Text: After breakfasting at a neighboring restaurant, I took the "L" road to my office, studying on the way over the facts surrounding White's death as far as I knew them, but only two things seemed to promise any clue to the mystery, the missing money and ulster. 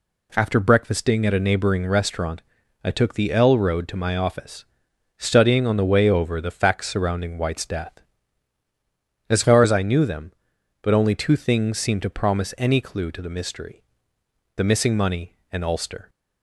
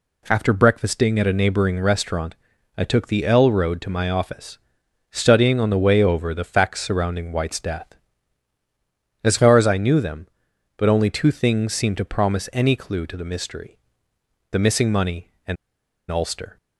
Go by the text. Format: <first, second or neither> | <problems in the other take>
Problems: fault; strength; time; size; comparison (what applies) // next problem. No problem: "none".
first | pauses between "and" and "ulster"; noticeable; at 15.5 s; 0.54 s long